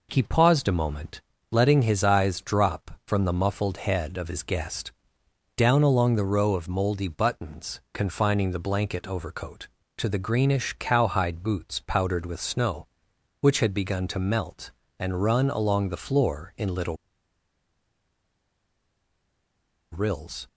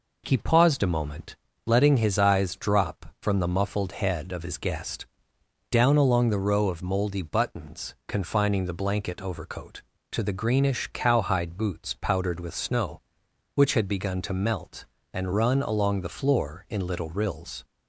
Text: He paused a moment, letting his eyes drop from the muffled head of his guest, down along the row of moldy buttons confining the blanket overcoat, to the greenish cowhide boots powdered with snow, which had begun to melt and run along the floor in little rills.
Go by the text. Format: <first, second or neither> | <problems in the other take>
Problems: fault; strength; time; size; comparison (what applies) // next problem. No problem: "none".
second | pauses between "little" and "rills"; strong; at 16.9 s; 2.9 s long